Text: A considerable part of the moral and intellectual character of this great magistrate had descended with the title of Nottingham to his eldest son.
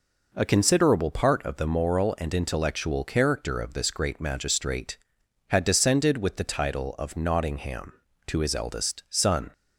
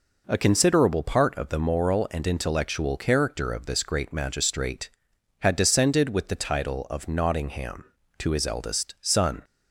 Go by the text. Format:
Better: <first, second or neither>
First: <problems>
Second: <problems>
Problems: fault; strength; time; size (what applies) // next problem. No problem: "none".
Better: neither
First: none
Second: none